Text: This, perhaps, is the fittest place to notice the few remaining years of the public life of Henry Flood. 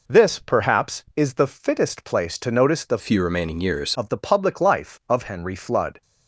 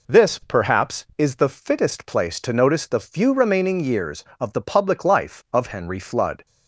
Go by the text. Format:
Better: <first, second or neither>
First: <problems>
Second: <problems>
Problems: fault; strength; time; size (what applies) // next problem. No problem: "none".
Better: second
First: changes voice from "few" to "years"; from 2.9 to 3.9 s; 1.0 s long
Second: none